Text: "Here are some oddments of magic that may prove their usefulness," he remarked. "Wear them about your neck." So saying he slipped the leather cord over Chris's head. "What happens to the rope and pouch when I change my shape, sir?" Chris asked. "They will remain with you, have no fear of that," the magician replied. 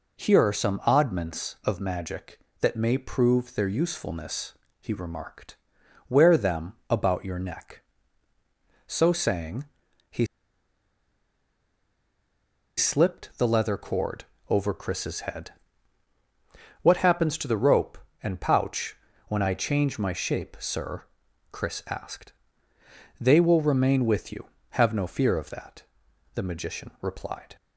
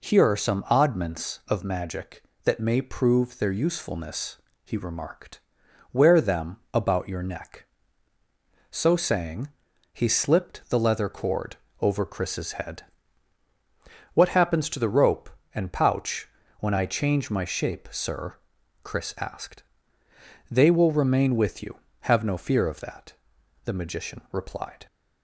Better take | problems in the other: second | pauses between "them" and "about"; slight; at 6.7 s; 0.16 s long; slight in the second // pauses between "saying" and "he"; at 9.6 s; 0.44 s long; also in the second // pauses between "he" and "slipped"; strong; at 10.2 s; 2.5 s long // pauses between "cord" and "over"; slight; at 14.2 s; 0.24 s long; slight in the second // pauses between "pouch" and "when"; slight; at 18.9 s; 0.30 s long; slight in the second

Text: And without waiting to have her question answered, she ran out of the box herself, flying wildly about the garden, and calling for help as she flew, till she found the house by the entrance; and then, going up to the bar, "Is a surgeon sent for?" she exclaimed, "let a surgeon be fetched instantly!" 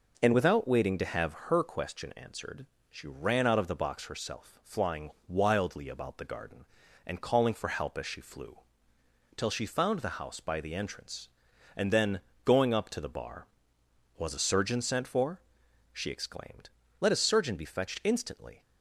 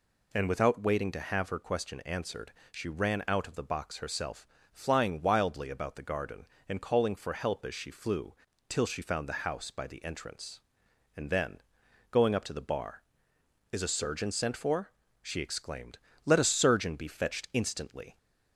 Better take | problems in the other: second | pauses between "flying" and "wildly"; slight; at 5.0 s; 0.18 s long // says "Was" for "Is"; at 14.1 s

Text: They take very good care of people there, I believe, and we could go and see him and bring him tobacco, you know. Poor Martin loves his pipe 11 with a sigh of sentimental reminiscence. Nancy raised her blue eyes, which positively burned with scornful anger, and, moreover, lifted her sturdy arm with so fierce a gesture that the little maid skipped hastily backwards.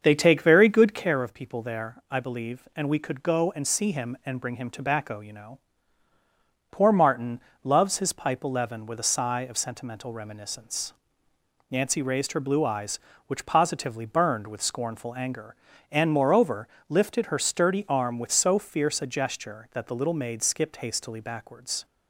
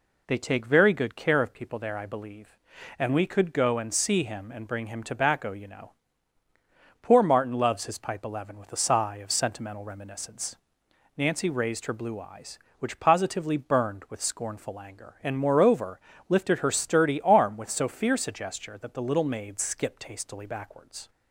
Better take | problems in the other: second | starts louder than the rest; until 1.2 s; 6.5 dB // pauses between "Martin" and "loves"; slight; at 7.3 s; 0.24 s long

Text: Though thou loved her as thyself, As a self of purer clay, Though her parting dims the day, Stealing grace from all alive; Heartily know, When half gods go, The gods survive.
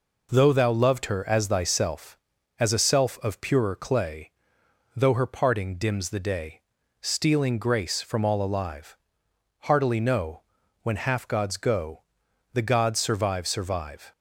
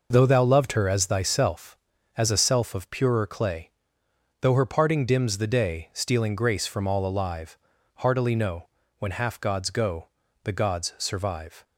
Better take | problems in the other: second | says "survive" twice; at 13.4 s

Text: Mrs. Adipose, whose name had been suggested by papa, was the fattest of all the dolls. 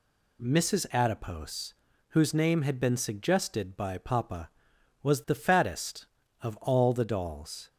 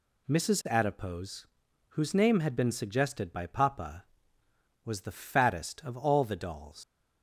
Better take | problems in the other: first | leaves "dolls" unfinished; at 6.8 s; 140 ms

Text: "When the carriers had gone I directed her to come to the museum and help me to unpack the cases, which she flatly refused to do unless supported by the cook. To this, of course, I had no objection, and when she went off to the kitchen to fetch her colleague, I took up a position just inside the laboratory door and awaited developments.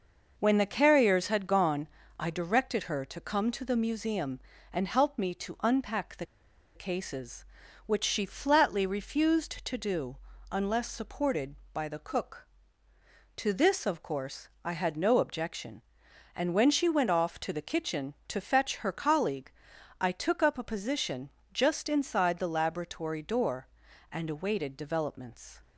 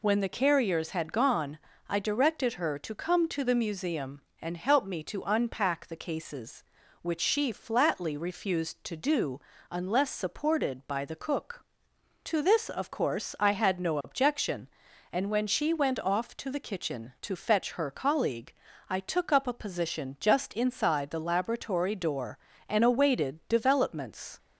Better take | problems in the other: second | pauses between "gone" and "I"; slight; at 1.8 s; 0.32 s long; slight in the second // pauses between "the" and "cases"; noticeable; at 6.2 s; 0.49 s long // pauses between "do" and "unless"; slight; at 10.1 s; 0.34 s long; slight in the second // pauses between "position" and "just"; slight; at 21.3 s; 0.20 s long

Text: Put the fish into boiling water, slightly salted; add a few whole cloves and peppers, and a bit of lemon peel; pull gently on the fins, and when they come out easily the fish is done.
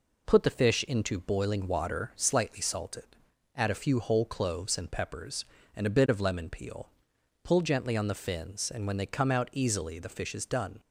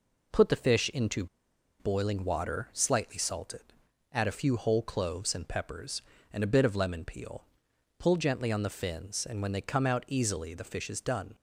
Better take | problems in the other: first | pauses between "into" and "boiling"; noticeable; at 1.2 s; 0.54 s long

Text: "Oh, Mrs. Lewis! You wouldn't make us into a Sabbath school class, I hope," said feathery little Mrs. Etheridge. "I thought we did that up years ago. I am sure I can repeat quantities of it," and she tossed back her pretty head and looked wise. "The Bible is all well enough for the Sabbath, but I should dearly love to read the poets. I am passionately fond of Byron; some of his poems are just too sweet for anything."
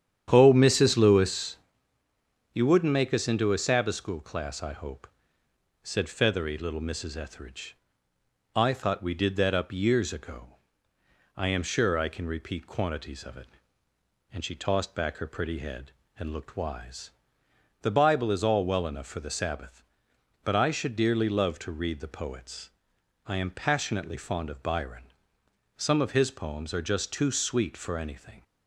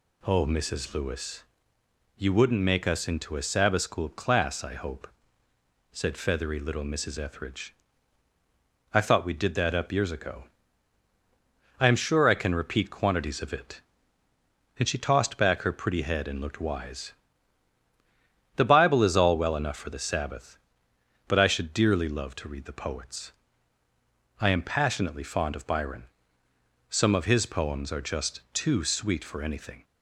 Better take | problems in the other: second | starts louder than the rest; strong; until 1.7 s; 9.5 dB

